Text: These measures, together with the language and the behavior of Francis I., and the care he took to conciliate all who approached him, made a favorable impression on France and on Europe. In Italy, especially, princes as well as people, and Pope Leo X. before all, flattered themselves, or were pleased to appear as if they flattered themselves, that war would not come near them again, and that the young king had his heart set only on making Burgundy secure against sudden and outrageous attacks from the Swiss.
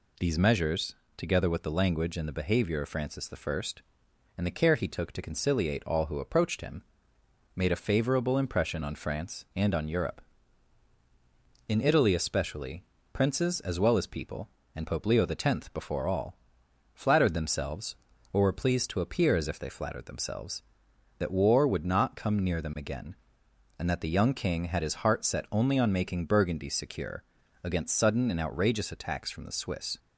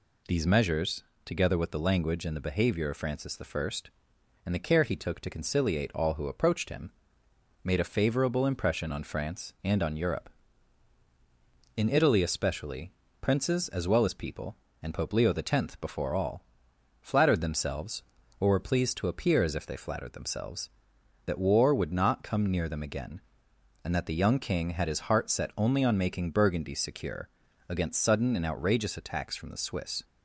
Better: neither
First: pauses between "secure" and "against"; at 27.2 s; 0.40 s long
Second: pauses between "secure" and "against"; at 27.2 s; 0.40 s long

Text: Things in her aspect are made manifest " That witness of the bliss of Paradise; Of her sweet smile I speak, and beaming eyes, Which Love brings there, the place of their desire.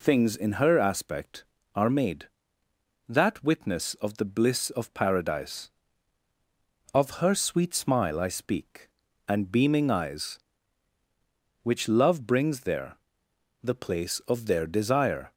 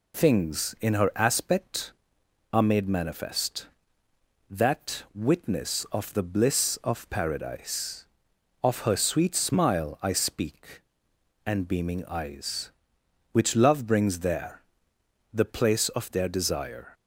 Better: second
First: skips "manifest"; at 2.4 s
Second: none

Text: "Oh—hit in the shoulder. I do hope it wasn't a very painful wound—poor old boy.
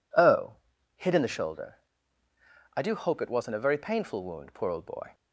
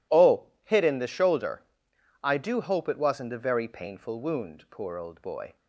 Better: neither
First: none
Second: none

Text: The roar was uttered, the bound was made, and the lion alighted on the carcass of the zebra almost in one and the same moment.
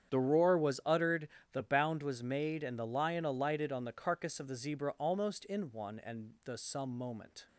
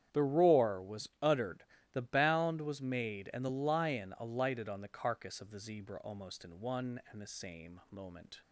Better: second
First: starts louder than the rest; strong; until 1.1 s; 8.5 dB // says "some" for "same"; at 6.5 s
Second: starts louder than the rest; strong; until 1.2 s; 9.5 dB

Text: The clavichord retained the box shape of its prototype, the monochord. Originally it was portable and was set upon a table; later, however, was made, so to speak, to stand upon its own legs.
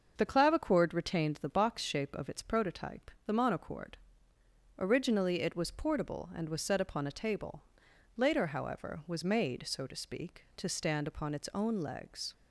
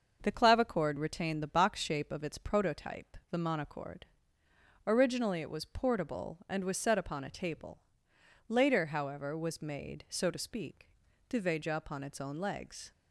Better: first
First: starts louder than the rest; until 1.1 s; 6.5 dB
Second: starts louder than the rest; until 1.2 s; 6.5 dB // says "veja" for "stand"; at 11.4 s

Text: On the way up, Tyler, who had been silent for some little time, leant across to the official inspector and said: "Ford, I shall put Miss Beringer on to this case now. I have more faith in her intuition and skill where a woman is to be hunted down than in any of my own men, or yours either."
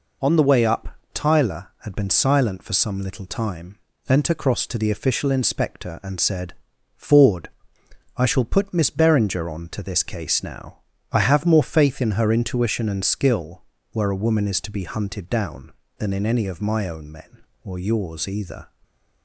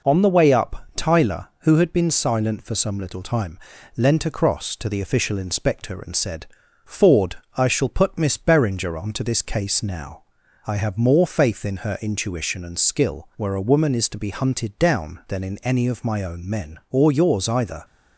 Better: second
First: skips "who"; at 1.7 s // pauses between "skill" and "where"; slight; at 13.6 s; 0.30 s long // stays silent after the last word; slight; from 18.6 s on; 0.6 s long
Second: none

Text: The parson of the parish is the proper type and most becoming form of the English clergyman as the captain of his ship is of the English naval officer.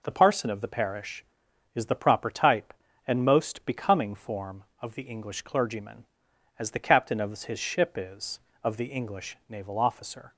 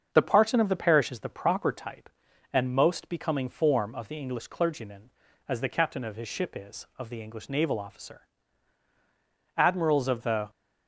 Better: first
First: none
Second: starts louder than the rest; until 1.1 s; 6.5 dB // goes on to say "Admirals of the"; noticeable; from 9.5 s on; 0.94 s long

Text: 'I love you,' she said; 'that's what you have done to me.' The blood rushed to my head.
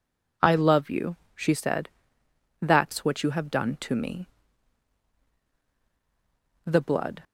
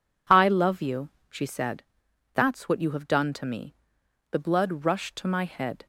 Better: second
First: stops before "rushed to my head"; at 7.2 s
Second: none

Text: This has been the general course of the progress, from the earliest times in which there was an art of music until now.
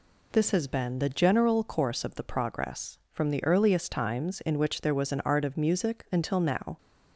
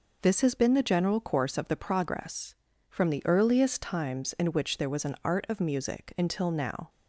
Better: neither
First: none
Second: none

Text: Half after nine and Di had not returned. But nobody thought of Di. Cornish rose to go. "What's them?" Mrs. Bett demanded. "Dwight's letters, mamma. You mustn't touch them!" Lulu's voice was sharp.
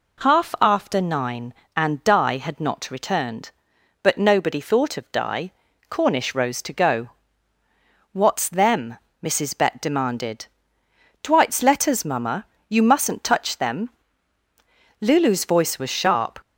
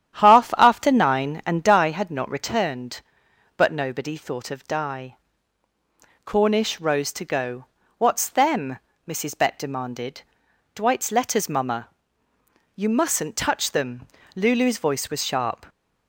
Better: first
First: none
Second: starts louder than the rest; strong; until 2.0 s; 10 dB

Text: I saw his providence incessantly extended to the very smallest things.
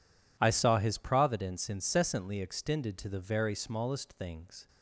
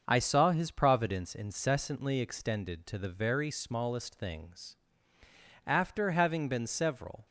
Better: first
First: none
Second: starts louder than the rest; until 1.0 s; 6.5 dB // goes on to say "After having been several"; from 5.6 s on; 1.5 s long

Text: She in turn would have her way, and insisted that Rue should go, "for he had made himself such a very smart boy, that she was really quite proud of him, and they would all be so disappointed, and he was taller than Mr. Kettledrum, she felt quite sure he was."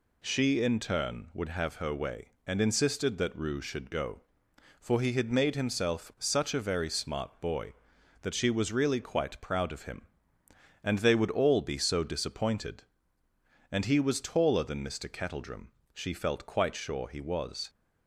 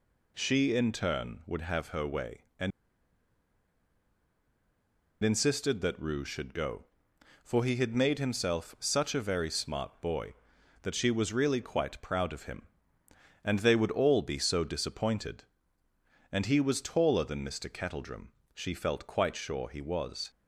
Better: first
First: none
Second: pauses between "and" and "insisted"; strong; at 2.7 s; 2.5 s long

